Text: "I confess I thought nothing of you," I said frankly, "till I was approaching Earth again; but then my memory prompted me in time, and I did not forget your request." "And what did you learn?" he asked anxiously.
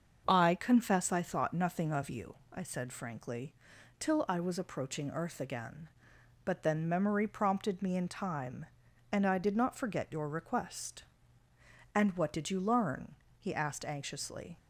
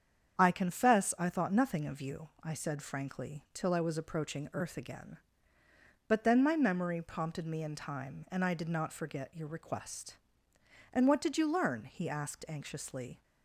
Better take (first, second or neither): second